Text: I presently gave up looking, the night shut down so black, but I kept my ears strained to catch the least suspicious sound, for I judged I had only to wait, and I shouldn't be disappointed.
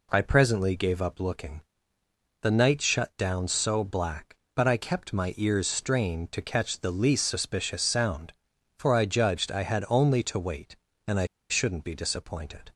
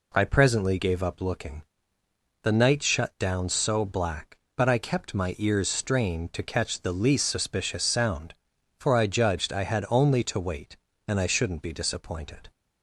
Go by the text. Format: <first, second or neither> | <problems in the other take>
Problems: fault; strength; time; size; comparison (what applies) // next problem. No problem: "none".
second | pauses between "I" and "shouldn't"; slight; at 11.2 s; 0.24 s long